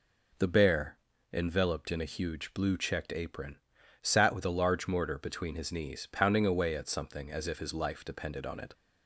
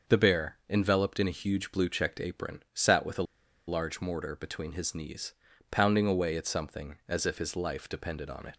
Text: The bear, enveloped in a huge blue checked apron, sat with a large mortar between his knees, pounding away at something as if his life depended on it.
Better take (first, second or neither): first